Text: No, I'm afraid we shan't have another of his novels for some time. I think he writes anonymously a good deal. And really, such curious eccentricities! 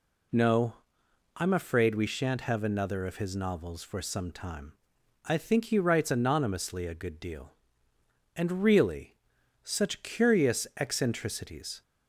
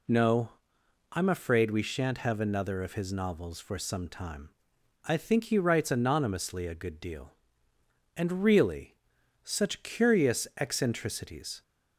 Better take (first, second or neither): neither